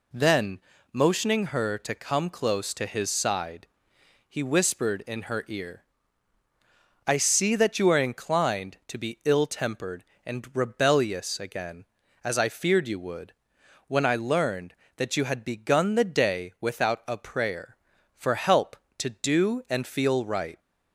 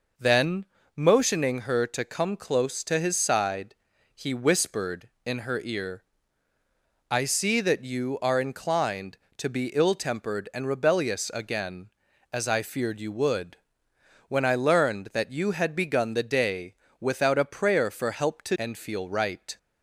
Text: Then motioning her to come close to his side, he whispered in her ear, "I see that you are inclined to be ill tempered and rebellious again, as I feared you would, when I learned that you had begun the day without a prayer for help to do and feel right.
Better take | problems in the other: first | pauses between "Then" and "motioning"; slight; at 0.6 s; 0.30 s long; slight in the first // pauses between "day" and "without"; slight; at 16.7 s; 0.26 s long // skips "do"; at 18.5 s

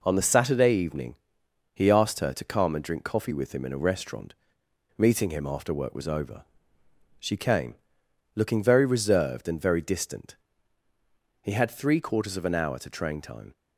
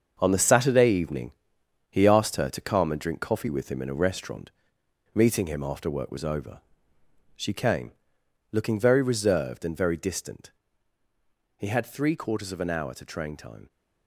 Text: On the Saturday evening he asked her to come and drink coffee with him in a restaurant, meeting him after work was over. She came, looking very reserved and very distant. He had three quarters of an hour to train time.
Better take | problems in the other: first | gets quieter; strong; throughout; 9.5 dB // pauses between "evening" and "he"; noticeable; at 1.2 s; 0.60 s long; noticeable in the first

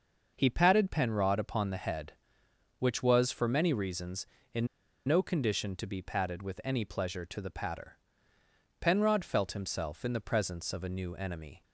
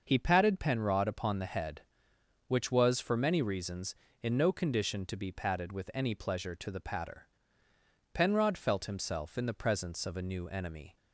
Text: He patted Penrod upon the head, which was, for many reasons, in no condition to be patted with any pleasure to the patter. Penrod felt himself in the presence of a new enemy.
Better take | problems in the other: second | starts louder than the rest; noticeable; until 1.3 s; 6 dB; noticeable in the second // pauses between "in" and "no"; at 4.6 s; 0.39 s long

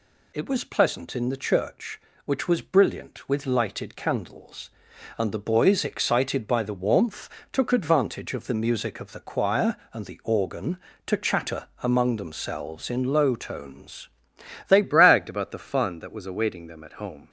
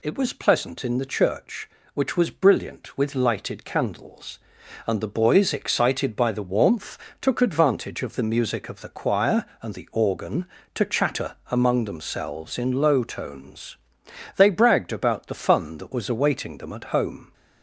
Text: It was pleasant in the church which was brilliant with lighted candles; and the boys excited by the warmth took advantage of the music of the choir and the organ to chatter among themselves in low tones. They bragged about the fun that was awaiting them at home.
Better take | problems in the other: second | pauses between "warmth" and "took"; slight; at 7.3 s; 0.20 s long; slight in the second // changes voice at "bragged"; from 14.8 s on; 2.4 s long

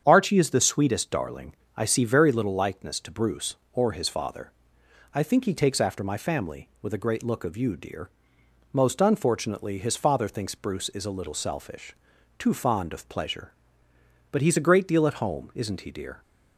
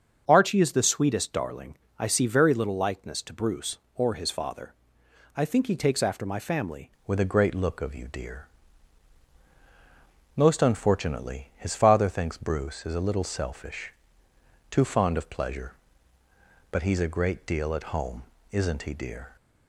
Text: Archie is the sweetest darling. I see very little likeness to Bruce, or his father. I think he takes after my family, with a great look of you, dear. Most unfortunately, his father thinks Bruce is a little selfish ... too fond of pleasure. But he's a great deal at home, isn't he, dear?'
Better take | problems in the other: first | starts louder than the rest; until 1.2 s; 7 dB; strong in the first // changes voice at "with"; from 7.0 s on; 12.3 s long

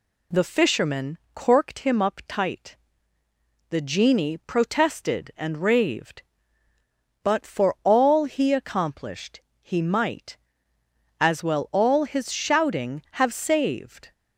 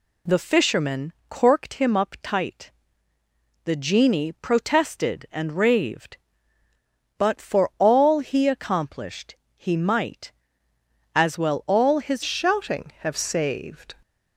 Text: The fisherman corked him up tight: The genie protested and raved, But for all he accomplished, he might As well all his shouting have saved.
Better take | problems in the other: first | pauses between "fisherman" and "corked"; slight; at 1.1 s; 0.16 s long; slight in the first // changes voice at "shouting"; from 12.2 s on; 1.7 s long

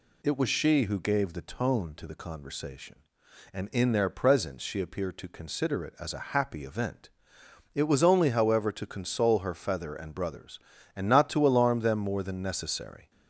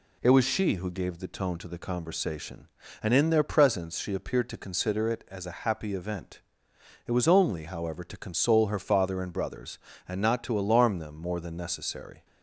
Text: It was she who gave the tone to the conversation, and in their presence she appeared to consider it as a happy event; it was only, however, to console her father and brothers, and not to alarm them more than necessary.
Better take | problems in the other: second | says "feather" for "father"; at 9.5 s

